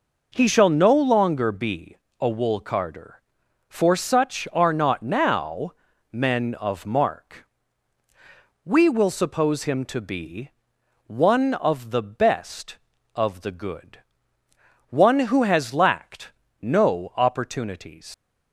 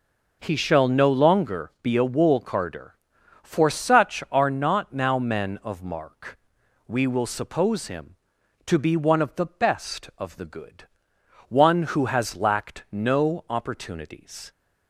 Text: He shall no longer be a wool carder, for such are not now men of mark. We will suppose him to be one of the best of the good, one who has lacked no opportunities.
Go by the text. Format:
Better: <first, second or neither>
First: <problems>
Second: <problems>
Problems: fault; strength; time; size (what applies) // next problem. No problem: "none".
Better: second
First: pauses between "be" and "a"; slight; at 1.9 s; 0.24 s long // pauses between "now" and "men"; at 5.7 s; 0.38 s long // pauses between "be" and "one"; noticeable; at 10.4 s; 0.56 s long // pauses between "lacked" and "no"; slight; at 16.3 s; 0.32 s long // leaves "opportunities" unfinished; at 18.1 s; 130 ms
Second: none